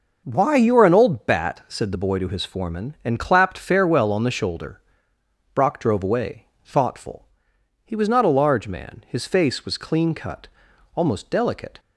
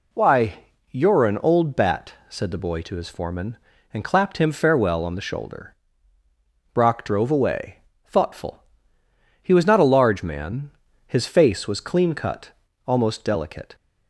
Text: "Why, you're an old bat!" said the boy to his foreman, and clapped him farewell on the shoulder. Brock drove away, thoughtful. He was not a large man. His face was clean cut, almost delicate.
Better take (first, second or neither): second